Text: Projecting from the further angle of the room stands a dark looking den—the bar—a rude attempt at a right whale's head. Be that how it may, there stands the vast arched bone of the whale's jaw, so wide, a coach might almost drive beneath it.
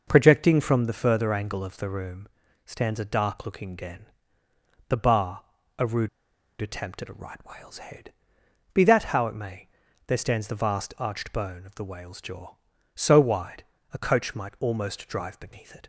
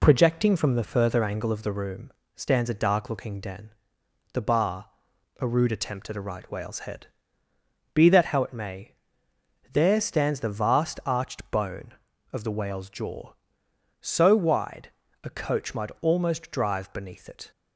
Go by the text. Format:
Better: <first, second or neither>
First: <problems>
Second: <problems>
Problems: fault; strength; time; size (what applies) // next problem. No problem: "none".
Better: second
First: pauses between "room" and "stands"; slight; at 2.2 s; 0.36 s long // pauses between "rude" and "attempt"; noticeable; at 6.0 s; 0.52 s long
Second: pauses between "room" and "stands"; slight; at 2.1 s; 0.22 s long